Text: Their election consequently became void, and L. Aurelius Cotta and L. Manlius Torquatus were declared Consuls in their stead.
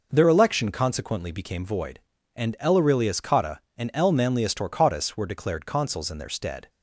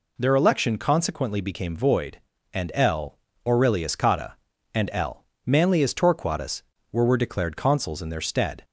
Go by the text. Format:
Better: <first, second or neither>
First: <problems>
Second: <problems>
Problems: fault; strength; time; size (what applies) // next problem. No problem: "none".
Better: first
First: none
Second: says "were" twice; at 7.0 s